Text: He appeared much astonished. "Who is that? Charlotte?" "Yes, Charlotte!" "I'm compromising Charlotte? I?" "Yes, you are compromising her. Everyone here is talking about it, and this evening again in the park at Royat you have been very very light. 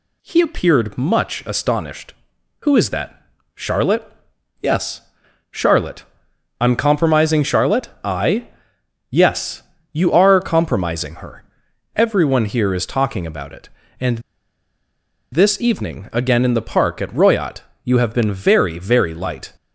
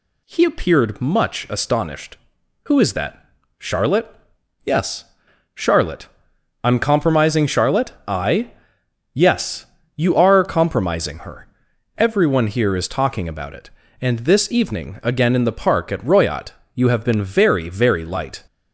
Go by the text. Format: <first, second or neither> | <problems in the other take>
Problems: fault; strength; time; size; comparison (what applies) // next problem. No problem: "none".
second | pauses between "and" and "this"; at 14.1 s; 1.1 s long // pauses between "Royat" and "you"; slight; at 17.6 s; 0.24 s long; slight in the second